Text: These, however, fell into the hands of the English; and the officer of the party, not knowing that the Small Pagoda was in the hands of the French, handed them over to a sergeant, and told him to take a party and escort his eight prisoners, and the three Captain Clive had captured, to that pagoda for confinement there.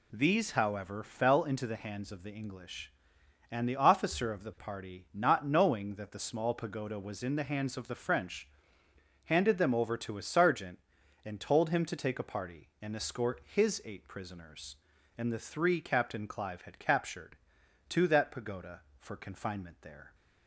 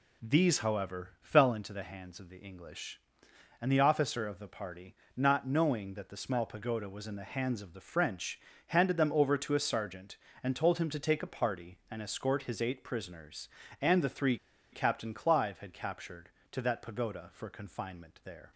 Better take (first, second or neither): first